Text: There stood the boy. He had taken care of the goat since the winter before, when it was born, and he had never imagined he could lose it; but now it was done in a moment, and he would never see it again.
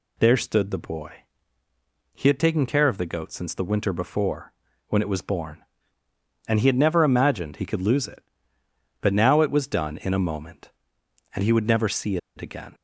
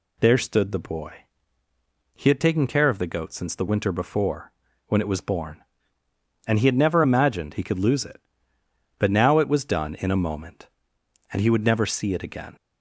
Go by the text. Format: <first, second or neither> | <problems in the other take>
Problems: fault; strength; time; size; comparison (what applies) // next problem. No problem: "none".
second | pauses between "see" and "it"; slight; at 12.1 s; 0.19 s long